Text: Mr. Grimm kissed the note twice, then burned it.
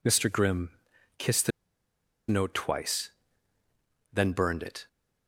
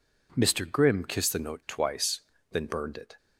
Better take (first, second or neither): second